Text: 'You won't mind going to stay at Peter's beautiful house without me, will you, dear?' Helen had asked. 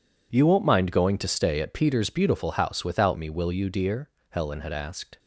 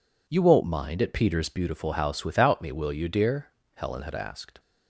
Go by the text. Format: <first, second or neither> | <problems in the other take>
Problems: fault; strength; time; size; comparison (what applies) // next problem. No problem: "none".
first | skips "going to stay"; at 1.0 s